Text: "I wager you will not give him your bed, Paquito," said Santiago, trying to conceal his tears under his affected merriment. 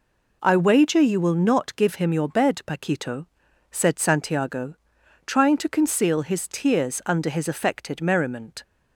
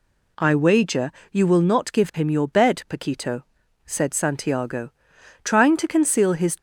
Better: first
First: none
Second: pauses between "wager" and "you"; slight; at 1.1 s; 0.20 s long // stops before "tears under his affected merriment"; at 6.5 s

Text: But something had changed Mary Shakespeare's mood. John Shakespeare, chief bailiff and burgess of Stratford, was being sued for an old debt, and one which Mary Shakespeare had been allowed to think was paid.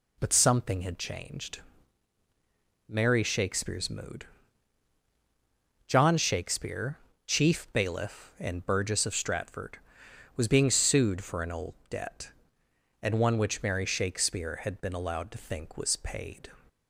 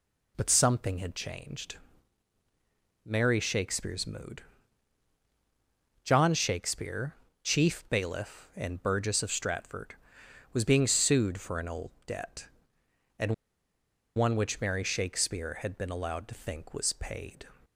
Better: first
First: pauses between "changed" and "Mary"; strong; at 1.5 s; 1.2 s long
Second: pauses between "changed" and "Mary"; strong; at 1.7 s; 1.2 s long // pauses between "and" and "one"; noticeable; at 13.3 s; 0.82 s long

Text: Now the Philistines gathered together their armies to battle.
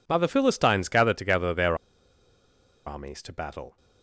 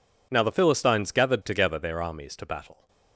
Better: second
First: pauses between "their" and "armies"; at 1.7 s; 1.1 s long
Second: none

